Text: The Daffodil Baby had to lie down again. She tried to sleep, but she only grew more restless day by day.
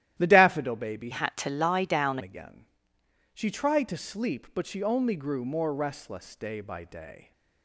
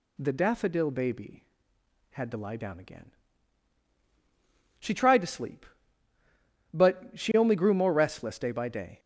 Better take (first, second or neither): second